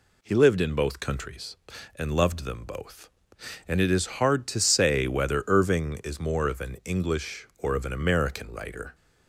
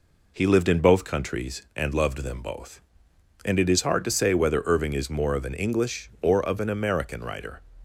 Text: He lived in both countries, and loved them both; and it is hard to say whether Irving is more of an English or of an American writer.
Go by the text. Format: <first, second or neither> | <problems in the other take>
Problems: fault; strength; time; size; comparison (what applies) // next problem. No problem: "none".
neither | none